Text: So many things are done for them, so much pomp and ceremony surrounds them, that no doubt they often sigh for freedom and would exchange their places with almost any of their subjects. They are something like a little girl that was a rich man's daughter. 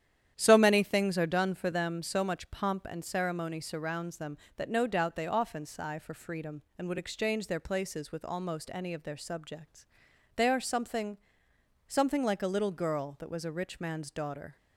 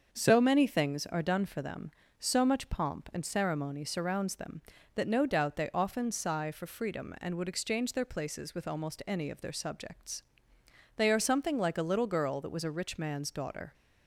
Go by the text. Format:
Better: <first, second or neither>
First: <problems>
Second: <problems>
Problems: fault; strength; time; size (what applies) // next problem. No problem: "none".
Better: second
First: starts louder than the rest; strong; until 1.3 s; 10 dB // says "something" twice; at 11.8 s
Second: starts louder than the rest; until 1.1 s; 6.5 dB